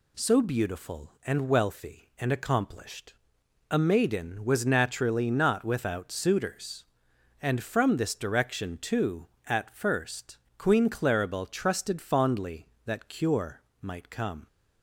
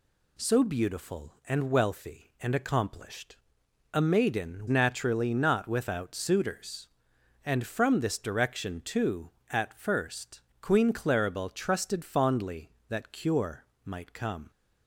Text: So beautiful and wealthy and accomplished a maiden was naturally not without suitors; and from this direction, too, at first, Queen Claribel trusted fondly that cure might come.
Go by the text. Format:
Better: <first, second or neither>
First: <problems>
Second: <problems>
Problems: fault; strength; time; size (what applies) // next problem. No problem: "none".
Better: first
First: pauses between "accomplished" and "a"; noticeable; at 3.1 s; 0.54 s long // pauses between "cure" and "might"; slight; at 13.6 s; 0.20 s long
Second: pauses between "accomplished" and "a"; noticeable; at 3.3 s; 0.54 s long // skips "was"; at 4.6 s // pauses between "cure" and "might"; slight; at 13.6 s; 0.20 s long